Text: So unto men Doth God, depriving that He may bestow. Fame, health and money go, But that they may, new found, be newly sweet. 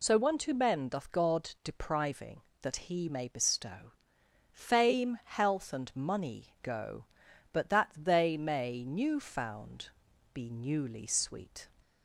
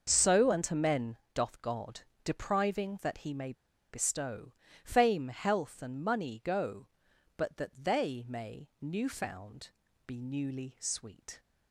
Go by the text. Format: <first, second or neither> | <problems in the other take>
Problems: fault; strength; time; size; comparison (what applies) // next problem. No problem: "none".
first | starts louder than the rest; until 1.0 s; 6 dB // pauses between "men" and "Doth"; slight; at 1.1 s; 0.16 s long // pauses between "may" and "bestow"; at 3.5 s; 0.38 s long